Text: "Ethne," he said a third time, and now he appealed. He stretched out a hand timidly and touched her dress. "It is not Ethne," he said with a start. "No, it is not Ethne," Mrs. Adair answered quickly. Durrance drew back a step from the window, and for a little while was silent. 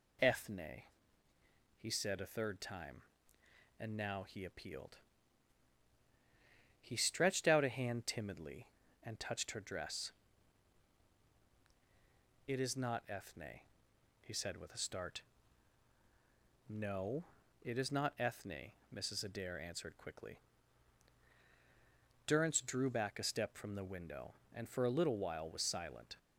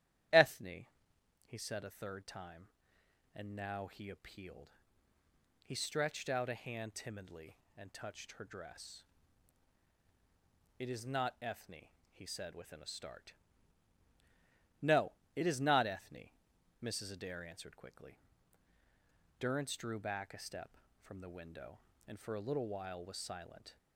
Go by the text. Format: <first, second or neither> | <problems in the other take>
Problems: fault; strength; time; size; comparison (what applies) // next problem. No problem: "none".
first | starts louder than the rest; strong; until 1.9 s; 11.5 dB // says "within" for "with"; at 12.5 s